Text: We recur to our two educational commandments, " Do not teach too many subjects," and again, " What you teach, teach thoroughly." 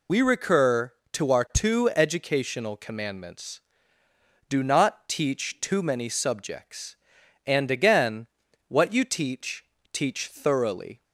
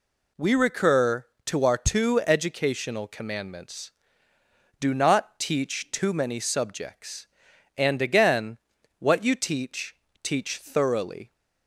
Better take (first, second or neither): second